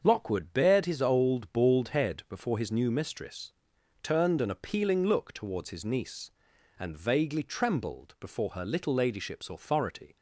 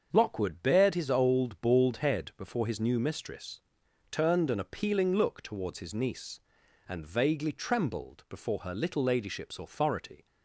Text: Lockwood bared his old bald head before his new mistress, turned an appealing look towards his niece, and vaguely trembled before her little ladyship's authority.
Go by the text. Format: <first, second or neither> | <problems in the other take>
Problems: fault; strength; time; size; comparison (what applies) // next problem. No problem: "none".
neither | starts louder than the rest; the same in both